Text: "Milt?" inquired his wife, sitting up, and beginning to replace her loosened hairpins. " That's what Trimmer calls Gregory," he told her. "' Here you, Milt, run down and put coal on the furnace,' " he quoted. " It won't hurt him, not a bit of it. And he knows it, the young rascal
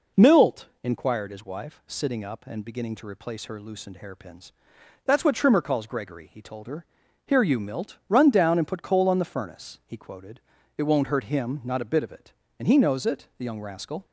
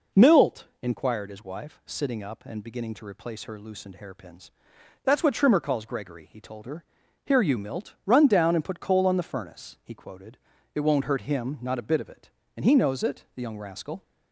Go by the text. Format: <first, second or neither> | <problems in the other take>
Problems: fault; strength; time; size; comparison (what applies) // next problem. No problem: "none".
neither | none